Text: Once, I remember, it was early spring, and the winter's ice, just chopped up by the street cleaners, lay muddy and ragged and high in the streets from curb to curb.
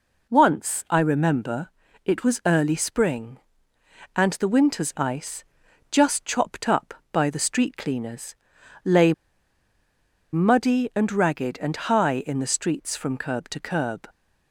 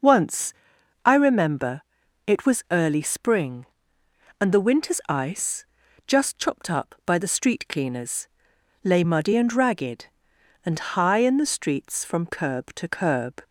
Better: second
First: pauses between "lay" and "muddy"; at 9.1 s; 1.1 s long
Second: none

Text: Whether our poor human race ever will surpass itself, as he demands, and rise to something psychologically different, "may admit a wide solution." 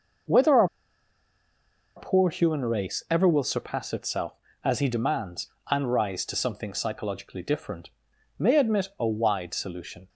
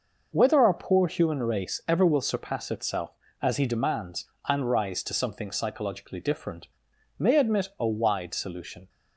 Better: second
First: pauses between "our" and "poor"; strong; at 0.6 s; 1.2 s long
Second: none

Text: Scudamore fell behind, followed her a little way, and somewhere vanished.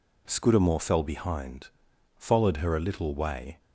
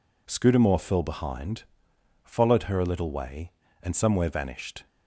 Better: second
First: stops before "and somewhere vanished"; at 3.5 s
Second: none

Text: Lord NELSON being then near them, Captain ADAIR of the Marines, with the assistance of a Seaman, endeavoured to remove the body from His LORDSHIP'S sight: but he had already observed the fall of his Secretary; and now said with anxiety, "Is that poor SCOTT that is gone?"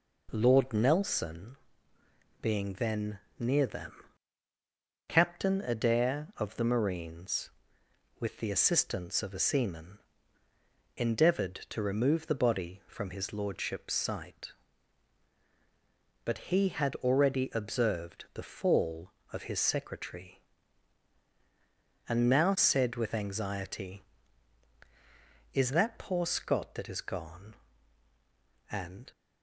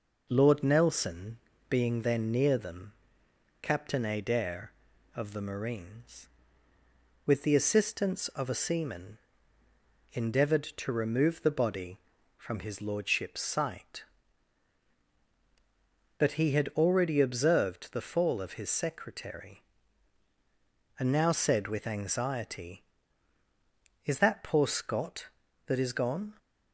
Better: second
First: pauses between "NELSON" and "being"; noticeable; at 1.5 s; 0.84 s long // pauses between "then" and "near"; slight; at 3.1 s; 0.22 s long // goes on to say "and"; slight; from 28.7 s on; 0.40 s long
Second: pauses between "NELSON" and "being"; slight; at 1.3 s; 0.32 s long

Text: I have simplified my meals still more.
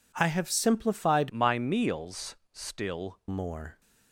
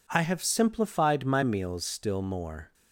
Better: second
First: changes voice from "my" to "still"; from 1.2 to 3.1 s; 1.9 s long // pauses between "meals" and "still"; slight; at 2.3 s; 0.16 s long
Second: none

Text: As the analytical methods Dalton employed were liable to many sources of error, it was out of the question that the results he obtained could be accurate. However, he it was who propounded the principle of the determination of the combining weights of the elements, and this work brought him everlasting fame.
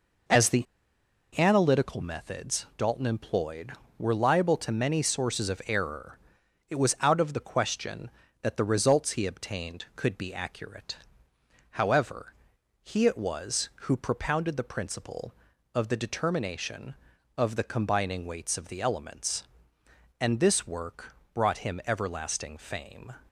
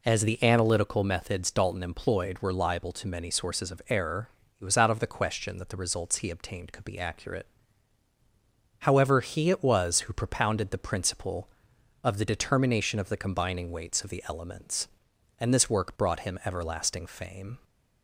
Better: second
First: pauses between "the" and "analytical"; noticeable; at 0.6 s; 0.74 s long // pauses between "work" and "brought"; slight; at 21.1 s; 0.18 s long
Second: none

